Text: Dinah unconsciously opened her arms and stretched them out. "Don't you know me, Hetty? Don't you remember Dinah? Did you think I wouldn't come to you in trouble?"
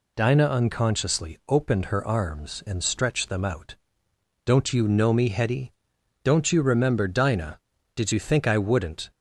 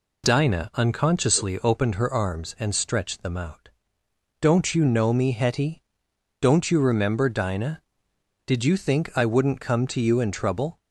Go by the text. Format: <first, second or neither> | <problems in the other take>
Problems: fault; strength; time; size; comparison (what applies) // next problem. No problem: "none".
second | stops before "come to you in trouble"; at 9.1 s